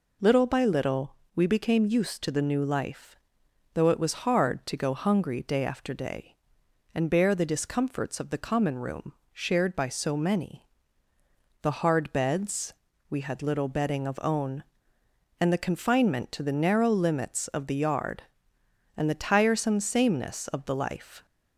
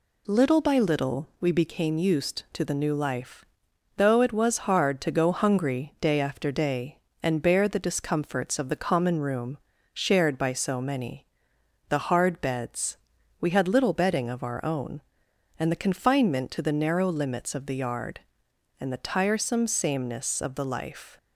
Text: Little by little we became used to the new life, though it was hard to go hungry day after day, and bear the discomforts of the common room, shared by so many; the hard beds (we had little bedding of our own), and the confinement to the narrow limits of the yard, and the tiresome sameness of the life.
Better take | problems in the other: second | pauses between "little" and "we"; slight; at 1.1 s; 0.20 s long // skips "our"; at 14.1 s

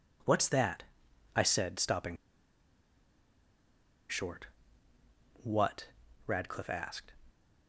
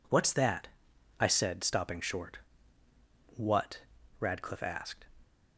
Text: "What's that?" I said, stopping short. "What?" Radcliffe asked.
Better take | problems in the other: second | pauses between "stopping" and "short"; strong; at 2.1 s; 1.9 s long

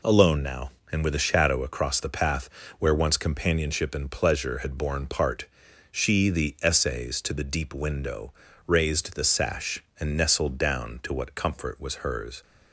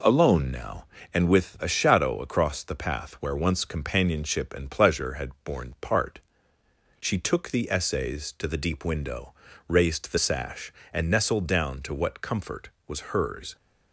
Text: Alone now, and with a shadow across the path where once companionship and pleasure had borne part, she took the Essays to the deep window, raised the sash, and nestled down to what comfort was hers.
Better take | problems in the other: second | pauses between "path" and "where"; slight; at 2.4 s; 0.30 s long // skips "took"; at 6.2 s

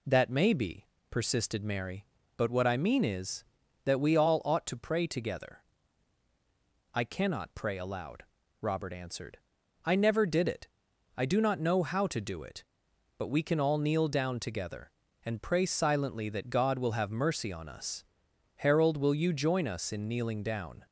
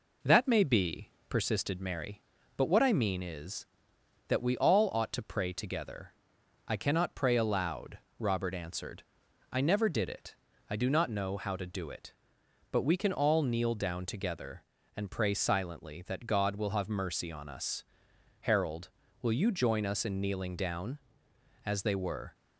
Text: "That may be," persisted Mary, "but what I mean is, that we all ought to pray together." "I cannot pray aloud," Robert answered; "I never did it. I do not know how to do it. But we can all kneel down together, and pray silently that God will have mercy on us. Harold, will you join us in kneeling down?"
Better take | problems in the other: first | goes on to say "As they were"; noticeable; from 21.6 s on; 0.70 s long

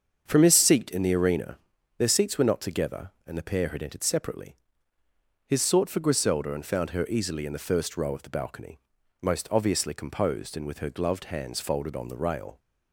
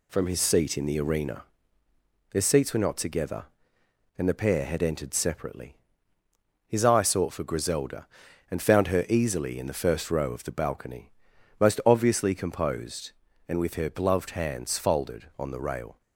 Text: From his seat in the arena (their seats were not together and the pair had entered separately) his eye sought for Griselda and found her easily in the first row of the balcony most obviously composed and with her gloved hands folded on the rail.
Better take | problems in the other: second | starts louder than the rest; until 1.2 s; 7 dB // skips "eye"; at 5.6 s // pauses between "balcony" and "most"; at 8.8 s; 0.40 s long; noticeable in the second

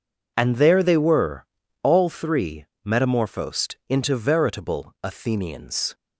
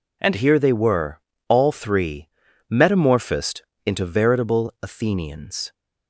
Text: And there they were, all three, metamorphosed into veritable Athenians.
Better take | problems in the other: first | says "here" for "there"; at 0.3 s // pauses between "metamorphosed" and "into"; slight; at 3.6 s; 0.22 s long

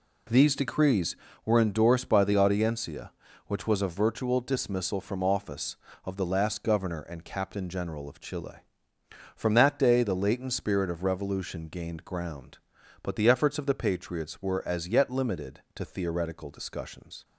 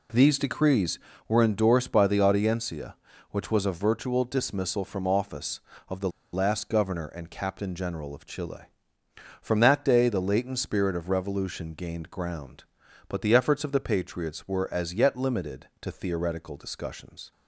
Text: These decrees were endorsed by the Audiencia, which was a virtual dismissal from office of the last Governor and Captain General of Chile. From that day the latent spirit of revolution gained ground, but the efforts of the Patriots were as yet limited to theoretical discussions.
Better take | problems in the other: first | pauses between "the" and "last"; slight; at 6.0 s; 0.24 s long

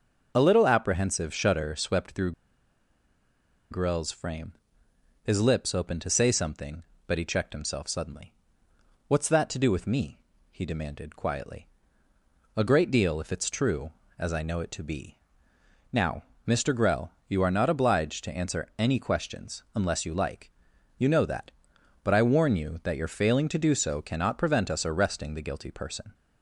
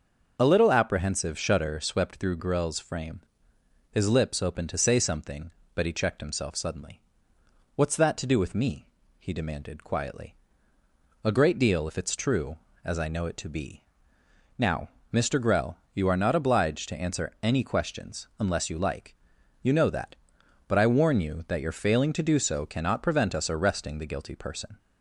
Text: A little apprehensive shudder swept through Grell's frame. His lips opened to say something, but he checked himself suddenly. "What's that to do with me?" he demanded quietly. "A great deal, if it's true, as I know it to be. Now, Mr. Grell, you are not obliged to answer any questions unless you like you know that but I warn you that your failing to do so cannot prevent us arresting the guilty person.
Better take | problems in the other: second | starts louder than the rest; until 1.3 s; 6 dB; also in the second // pauses between "through" and "Grell's"; strong; at 2.3 s; 1.3 s long // pauses between "like" and "you"; noticeable; at 20.5 s; 0.46 s long; noticeable in the second

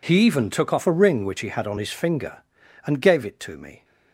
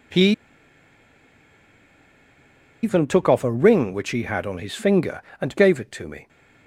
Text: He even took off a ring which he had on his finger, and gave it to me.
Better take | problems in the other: first | pauses between "He" and "even"; strong; at 0.2 s; 2.5 s long

